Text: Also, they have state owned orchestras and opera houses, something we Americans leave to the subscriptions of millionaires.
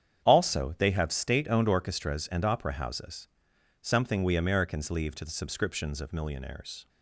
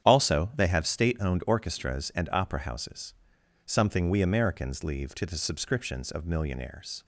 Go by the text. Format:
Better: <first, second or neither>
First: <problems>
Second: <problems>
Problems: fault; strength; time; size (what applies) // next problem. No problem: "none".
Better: neither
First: starts louder than the rest; strong; until 1.2 s; 8.5 dB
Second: starts louder than the rest; strong; until 1.1 s; 10 dB